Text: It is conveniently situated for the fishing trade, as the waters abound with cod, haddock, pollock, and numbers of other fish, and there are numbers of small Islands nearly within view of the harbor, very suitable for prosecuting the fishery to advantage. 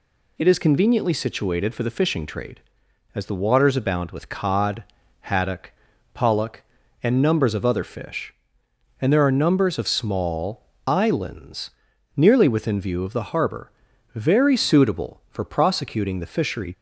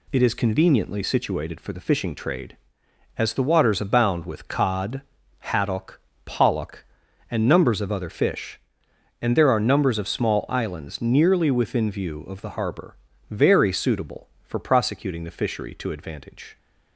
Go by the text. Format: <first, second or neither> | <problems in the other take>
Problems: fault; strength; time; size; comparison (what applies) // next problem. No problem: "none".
second | pauses between "small" and "Islands"; slight; at 10.6 s; 0.24 s long // pauses between "Islands" and "nearly"; noticeable; at 11.7 s; 0.46 s long // stops before "to advantage"; at 16.7 s